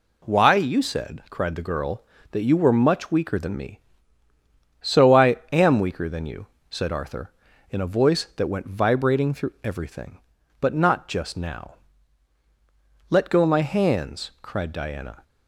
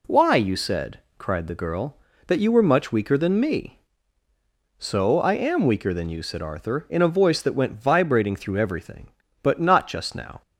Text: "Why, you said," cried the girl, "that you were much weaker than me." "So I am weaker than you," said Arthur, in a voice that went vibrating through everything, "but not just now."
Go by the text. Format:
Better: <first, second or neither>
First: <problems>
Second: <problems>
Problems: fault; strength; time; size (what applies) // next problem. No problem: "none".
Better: second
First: pauses between "I" and "am"; slight; at 5.3 s; 0.16 s long // goes on to say "Let go my hands cried Diana"; strong; from 13.0 s on; 2.1 s long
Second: none